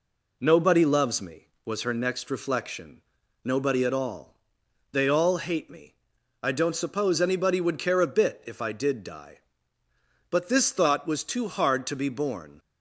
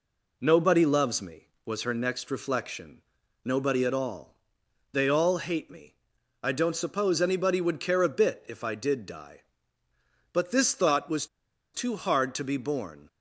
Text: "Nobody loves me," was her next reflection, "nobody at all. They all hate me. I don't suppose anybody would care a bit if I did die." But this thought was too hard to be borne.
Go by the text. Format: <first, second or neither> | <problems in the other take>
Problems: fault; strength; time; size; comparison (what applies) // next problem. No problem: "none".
first | pauses between "was" and "too"; noticeable; at 11.2 s; 0.48 s long